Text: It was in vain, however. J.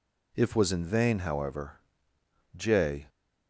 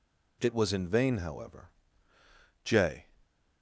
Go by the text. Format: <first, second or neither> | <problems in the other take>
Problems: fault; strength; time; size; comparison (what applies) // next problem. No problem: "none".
second | says "If" for "It"; at 0.3 s